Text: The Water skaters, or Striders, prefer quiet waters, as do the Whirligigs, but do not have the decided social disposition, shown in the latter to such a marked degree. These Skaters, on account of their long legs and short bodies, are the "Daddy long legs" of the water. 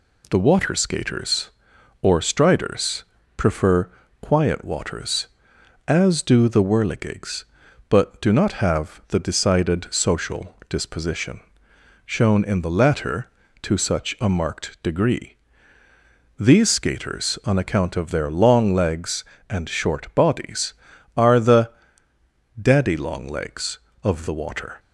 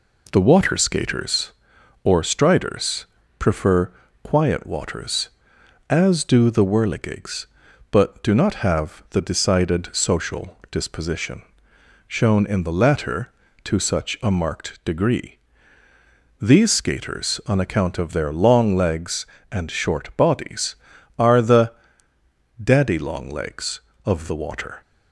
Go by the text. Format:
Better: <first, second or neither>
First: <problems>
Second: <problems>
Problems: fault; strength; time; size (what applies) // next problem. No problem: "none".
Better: first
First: pauses between "prefer" and "quiet"; slight; at 3.8 s; 0.32 s long // pauses between "the" and "Daddy"; noticeable; at 21.6 s; 0.90 s long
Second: starts louder than the rest; until 1.4 s; 3.5 dB // pauses between "prefer" and "quiet"; slight; at 3.9 s; 0.32 s long // pauses between "the" and "Daddy"; noticeable; at 21.7 s; 0.90 s long